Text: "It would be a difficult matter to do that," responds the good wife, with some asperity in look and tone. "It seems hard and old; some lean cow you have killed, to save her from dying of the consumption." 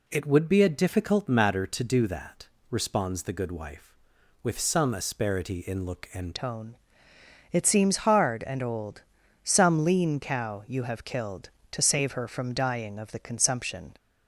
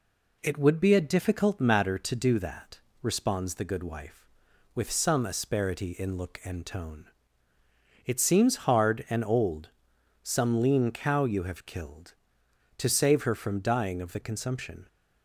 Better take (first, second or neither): second